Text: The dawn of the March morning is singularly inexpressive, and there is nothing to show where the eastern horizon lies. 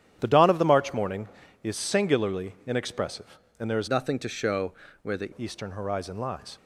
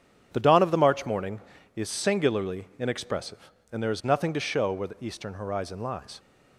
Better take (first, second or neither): second